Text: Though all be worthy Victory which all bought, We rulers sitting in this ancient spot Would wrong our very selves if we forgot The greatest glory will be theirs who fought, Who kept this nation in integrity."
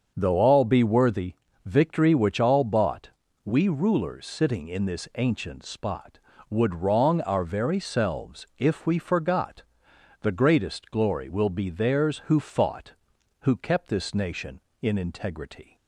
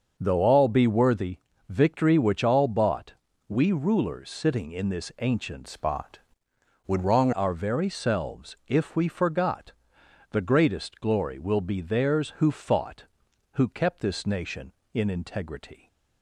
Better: first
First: starts louder than the rest; until 1.1 s; 6.5 dB // pauses between "worthy" and "Victory"; slight; at 1.3 s; 0.30 s long // pauses between "forgot" and "The"; noticeable; at 9.6 s; 0.58 s long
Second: starts louder than the rest; until 1.1 s; 6.5 dB // pauses between "worthy" and "Victory"; slight; at 1.3 s; 0.30 s long // changes voice from "spot" to "wrong"; from 5.6 to 7.3 s; 1.7 s long // pauses between "forgot" and "The"; noticeable; at 9.7 s; 0.58 s long

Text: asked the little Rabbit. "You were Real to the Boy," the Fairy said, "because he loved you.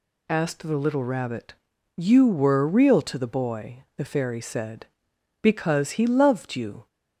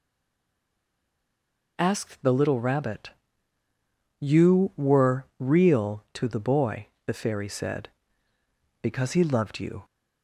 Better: first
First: none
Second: stays silent before the first word; noticeable; until 1.7 s; 1.7 s long

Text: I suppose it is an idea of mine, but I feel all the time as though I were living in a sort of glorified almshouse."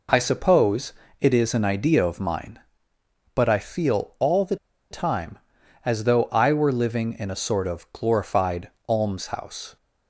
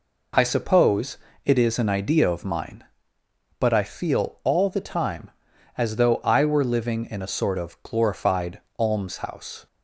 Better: second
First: pauses between "suppose" and "it"; slight; at 0.9 s; 0.28 s long // pauses between "the" and "time"; slight; at 4.5 s; 0.35 s long // pauses between "glorified" and "almshouse"; slight; at 8.6 s; 0.20 s long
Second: pauses between "suppose" and "it"; slight; at 1.1 s; 0.28 s long // pauses between "glorified" and "almshouse"; slight; at 8.5 s; 0.20 s long

